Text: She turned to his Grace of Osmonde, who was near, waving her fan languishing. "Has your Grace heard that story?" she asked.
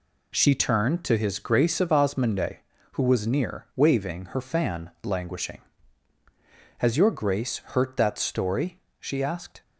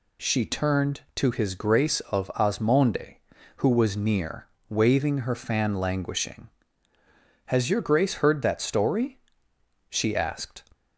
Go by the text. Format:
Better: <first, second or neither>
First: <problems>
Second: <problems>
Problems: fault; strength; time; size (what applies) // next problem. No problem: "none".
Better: second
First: says "hurt" for "heard"; at 7.5 s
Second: none